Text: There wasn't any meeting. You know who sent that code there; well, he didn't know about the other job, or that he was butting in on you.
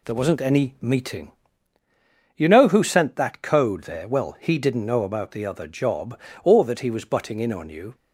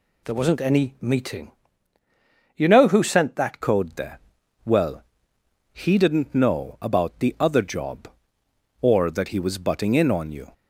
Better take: first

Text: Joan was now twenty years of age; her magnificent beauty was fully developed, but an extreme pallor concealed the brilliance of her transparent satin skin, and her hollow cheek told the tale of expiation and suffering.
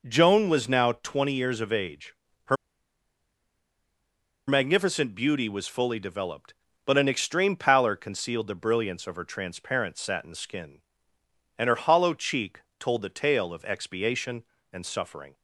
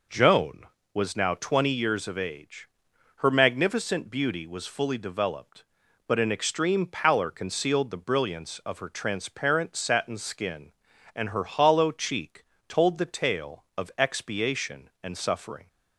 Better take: second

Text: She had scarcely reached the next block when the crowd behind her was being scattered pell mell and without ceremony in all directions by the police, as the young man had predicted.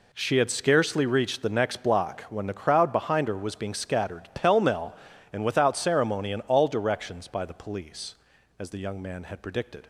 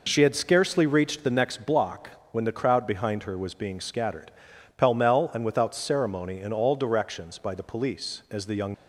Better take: first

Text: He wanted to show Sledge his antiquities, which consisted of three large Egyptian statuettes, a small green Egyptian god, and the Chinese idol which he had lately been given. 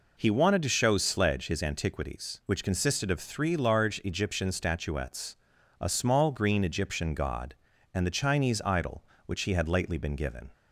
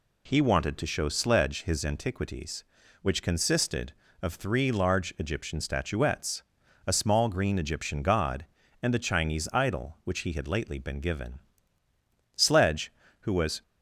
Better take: first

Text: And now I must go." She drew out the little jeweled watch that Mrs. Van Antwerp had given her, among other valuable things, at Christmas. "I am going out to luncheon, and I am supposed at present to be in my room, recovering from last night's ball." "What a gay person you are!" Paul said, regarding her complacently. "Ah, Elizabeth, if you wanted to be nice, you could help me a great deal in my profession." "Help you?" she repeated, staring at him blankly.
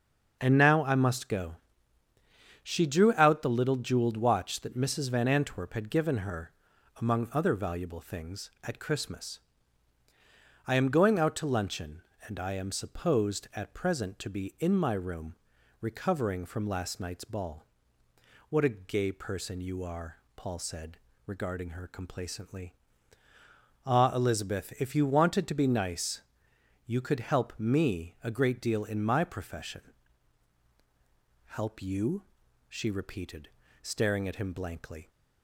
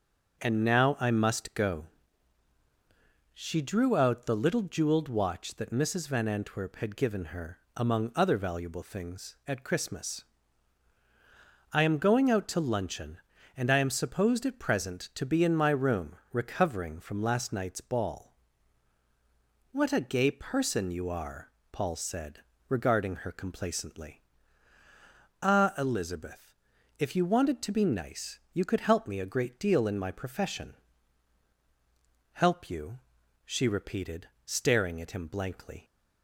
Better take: neither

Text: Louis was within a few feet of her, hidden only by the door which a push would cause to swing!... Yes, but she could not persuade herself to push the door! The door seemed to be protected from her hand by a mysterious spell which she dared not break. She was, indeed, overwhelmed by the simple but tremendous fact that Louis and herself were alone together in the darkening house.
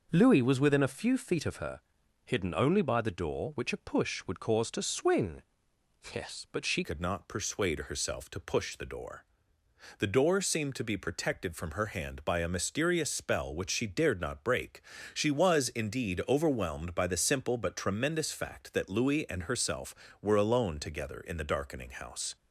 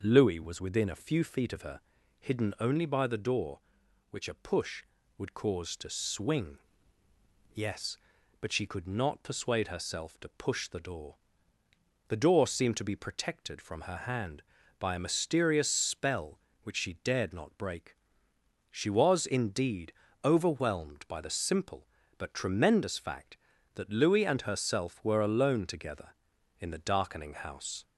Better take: second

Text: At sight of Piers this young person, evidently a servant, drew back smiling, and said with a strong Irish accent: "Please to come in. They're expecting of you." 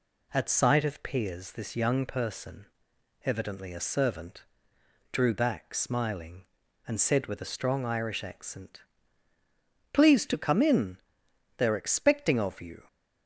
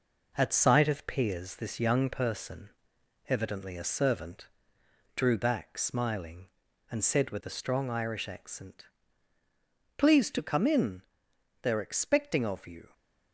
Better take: first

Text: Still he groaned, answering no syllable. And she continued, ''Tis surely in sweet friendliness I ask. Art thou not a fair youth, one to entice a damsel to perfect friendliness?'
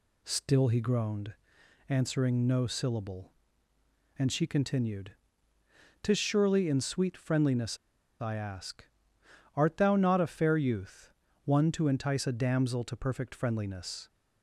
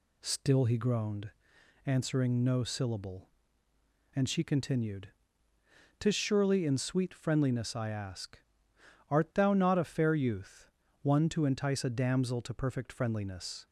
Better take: second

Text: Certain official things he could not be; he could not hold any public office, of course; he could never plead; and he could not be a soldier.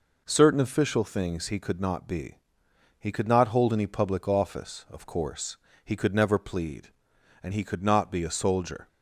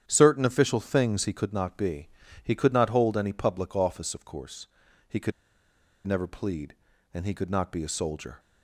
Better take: first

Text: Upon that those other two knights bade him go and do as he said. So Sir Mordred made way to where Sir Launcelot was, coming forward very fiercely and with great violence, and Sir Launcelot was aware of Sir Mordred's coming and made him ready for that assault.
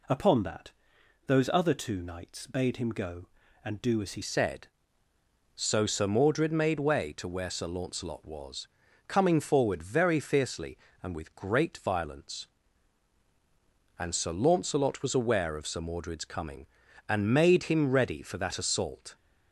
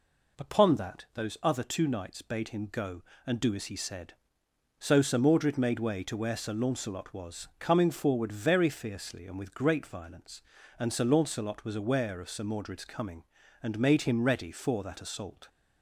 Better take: second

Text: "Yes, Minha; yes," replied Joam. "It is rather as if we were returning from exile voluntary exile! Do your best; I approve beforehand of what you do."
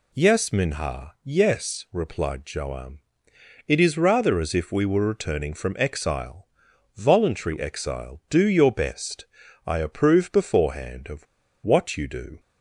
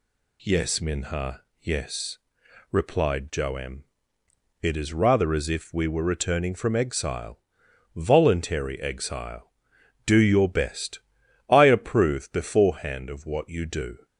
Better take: second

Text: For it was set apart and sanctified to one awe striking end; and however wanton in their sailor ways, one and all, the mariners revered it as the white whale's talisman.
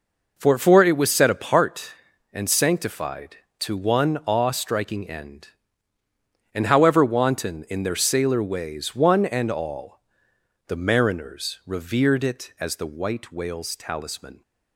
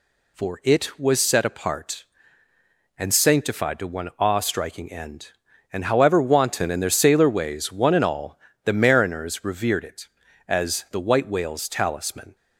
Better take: second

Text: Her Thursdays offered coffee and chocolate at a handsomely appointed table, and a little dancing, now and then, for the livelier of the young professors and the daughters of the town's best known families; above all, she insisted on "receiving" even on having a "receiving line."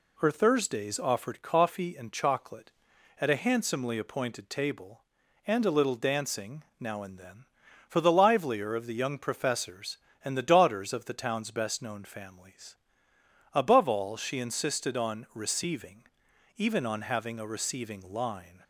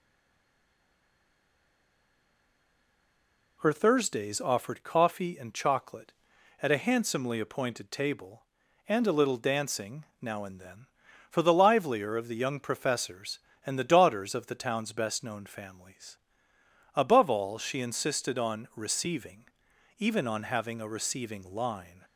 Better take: first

